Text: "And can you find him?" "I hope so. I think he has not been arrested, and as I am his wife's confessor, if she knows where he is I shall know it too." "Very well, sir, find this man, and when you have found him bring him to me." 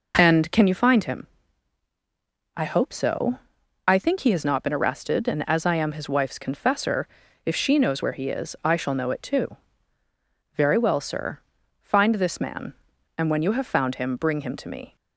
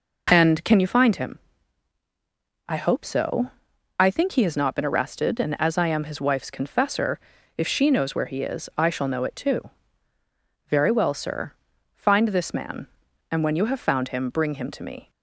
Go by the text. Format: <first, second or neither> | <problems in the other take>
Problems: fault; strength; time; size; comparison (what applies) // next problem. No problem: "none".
neither | none